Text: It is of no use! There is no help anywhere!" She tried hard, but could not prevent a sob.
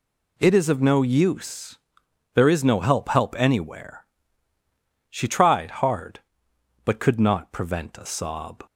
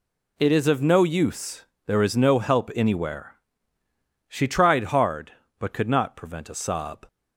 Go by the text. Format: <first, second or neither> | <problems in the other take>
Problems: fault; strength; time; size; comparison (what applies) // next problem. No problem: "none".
second | says "help" twice; at 3.0 s